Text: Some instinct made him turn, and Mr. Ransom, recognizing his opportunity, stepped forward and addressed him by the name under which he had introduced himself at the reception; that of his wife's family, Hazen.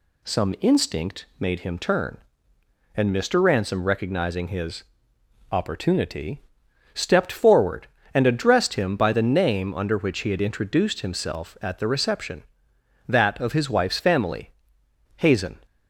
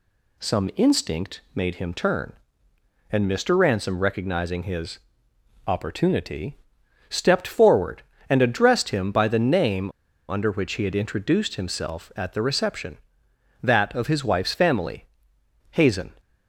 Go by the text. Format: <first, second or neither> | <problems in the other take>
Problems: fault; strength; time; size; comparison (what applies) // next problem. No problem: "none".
first | pauses between "his" and "opportunity"; noticeable; at 4.9 s; 0.68 s long; noticeable in the first // pauses between "name" and "under"; at 9.9 s; 0.37 s long